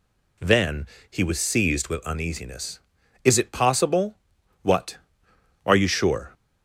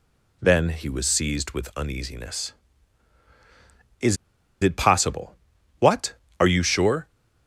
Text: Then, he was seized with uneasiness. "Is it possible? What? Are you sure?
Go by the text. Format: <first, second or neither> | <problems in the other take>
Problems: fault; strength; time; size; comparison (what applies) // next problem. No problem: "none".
first | pauses between "Is" and "it"; noticeable; at 4.1 s; 0.47 s long